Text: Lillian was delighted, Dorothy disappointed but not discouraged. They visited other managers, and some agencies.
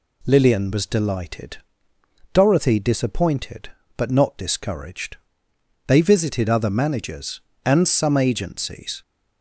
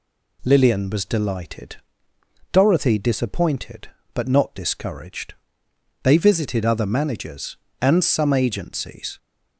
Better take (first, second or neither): neither